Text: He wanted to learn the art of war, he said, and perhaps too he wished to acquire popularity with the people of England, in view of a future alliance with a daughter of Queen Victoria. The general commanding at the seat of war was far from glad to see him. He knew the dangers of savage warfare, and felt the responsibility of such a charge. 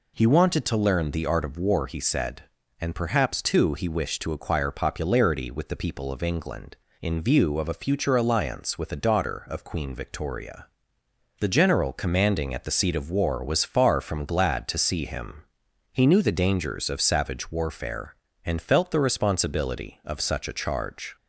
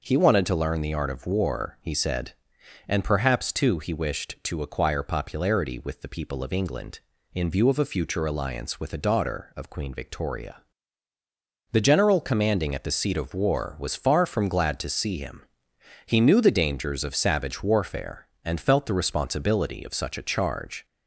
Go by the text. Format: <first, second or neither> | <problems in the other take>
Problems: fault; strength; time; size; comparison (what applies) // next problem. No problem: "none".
neither | none